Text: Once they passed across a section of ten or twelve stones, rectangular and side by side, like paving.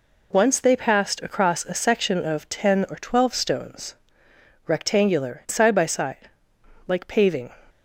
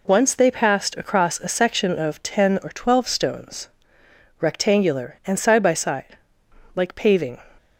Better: second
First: skips "and"; at 5.4 s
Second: none

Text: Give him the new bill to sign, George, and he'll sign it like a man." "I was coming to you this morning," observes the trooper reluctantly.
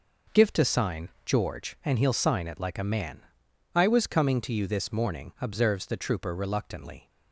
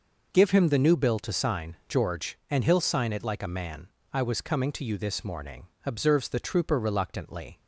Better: second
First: skips "him the new bill"; at 0.5 s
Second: none

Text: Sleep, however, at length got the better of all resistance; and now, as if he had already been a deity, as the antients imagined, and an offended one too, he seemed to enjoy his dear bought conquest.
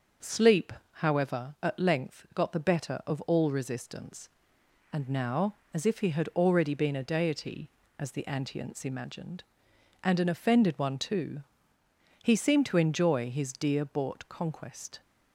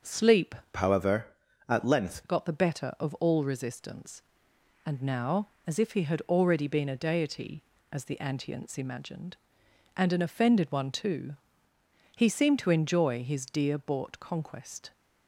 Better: first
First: starts louder than the rest; until 1.4 s; 6 dB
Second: starts louder than the rest; until 1.2 s; 6.5 dB // changes voice from "however" to "length"; from 0.7 to 2.2 s; 1.5 s long

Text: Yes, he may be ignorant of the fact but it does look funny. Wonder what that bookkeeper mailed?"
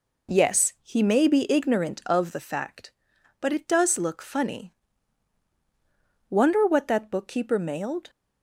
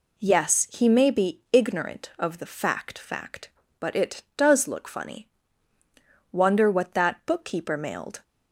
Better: first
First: none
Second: says "fact" twice; at 2.9 s

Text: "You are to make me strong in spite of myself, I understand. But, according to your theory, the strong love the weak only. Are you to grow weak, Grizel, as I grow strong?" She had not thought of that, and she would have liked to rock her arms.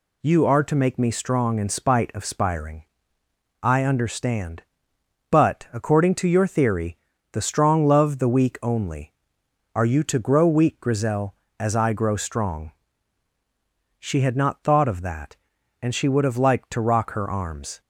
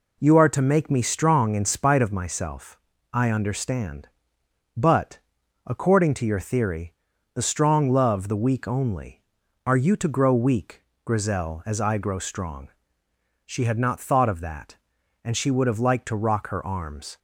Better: second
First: says "spiring" for "myself"; at 2.2 s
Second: none

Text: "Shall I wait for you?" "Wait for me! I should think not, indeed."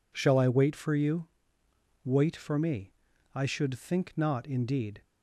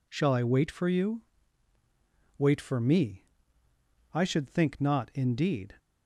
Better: neither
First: none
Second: none

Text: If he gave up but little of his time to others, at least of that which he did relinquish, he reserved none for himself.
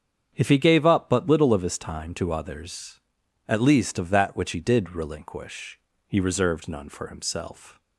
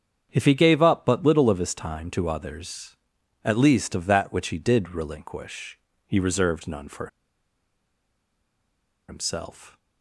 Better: first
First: starts louder than the rest; strong; until 1.3 s; 8 dB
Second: starts louder than the rest; strong; until 1.3 s; 8 dB // pauses between "for" and "himself"; strong; at 7.0 s; 2.0 s long

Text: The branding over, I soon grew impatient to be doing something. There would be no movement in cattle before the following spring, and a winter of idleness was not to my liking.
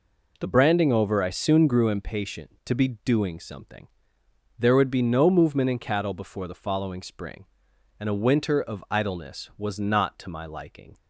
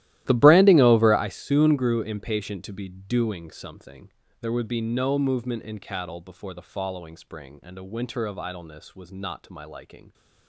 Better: first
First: none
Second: starts louder than the rest; strong; until 1.3 s; 14.5 dB

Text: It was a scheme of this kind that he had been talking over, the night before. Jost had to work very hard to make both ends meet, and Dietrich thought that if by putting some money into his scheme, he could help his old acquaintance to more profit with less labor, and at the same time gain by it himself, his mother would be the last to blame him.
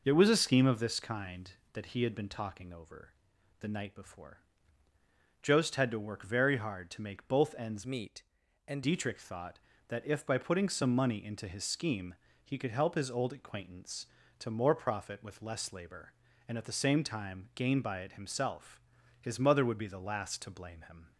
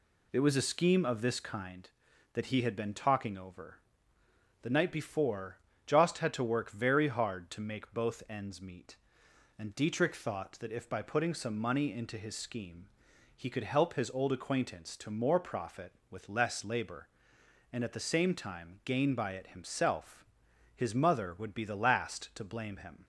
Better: second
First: changes voice from "meet" to "and"; from 7.8 to 8.8 s; 1.0 s long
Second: none

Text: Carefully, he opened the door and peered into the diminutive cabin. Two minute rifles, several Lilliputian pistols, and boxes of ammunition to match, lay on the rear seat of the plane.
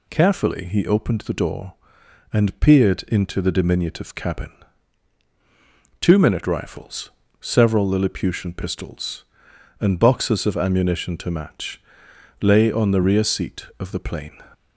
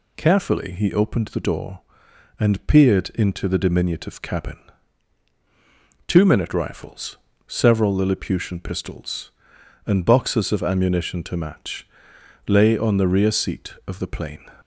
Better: neither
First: none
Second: none

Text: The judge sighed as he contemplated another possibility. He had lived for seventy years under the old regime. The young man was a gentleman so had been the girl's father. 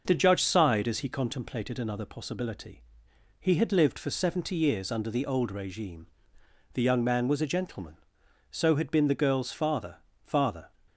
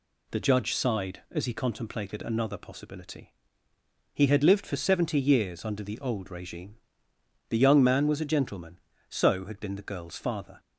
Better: second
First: says "father" twice; at 10.2 s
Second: none

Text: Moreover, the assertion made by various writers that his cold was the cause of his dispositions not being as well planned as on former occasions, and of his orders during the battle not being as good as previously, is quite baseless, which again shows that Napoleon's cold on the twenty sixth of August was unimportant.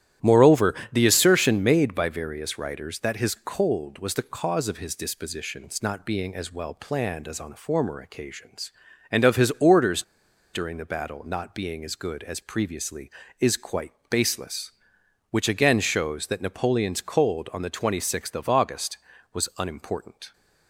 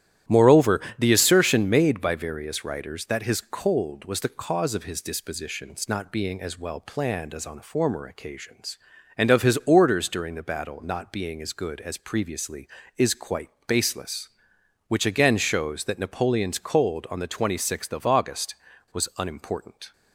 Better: second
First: starts louder than the rest; strong; until 1.4 s; 12 dB // pauses between "orders" and "during"; noticeable; at 10.0 s; 0.51 s long // pauses between "quite" and "baseless"; slight; at 13.9 s; 0.18 s long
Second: starts louder than the rest; strong; until 1.4 s; 12 dB // pauses between "quite" and "baseless"; slight; at 13.4 s; 0.18 s long

